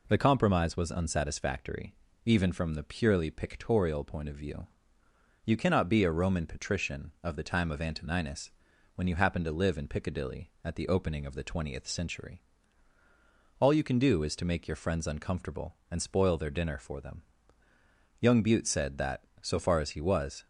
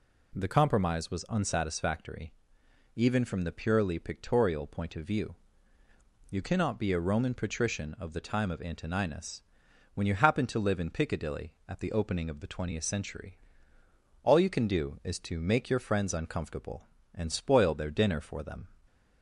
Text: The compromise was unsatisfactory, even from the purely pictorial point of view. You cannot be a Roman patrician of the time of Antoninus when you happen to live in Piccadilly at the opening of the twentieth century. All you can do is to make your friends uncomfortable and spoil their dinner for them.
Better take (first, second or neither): second